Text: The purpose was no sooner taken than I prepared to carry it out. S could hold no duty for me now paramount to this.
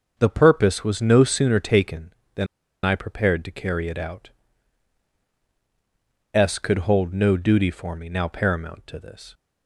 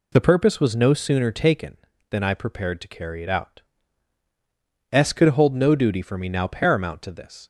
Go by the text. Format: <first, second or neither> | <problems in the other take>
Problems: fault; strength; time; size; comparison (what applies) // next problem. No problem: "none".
second | starts louder than the rest; until 1.2 s; 6.5 dB // pauses between "than" and "I"; at 2.4 s; 0.38 s long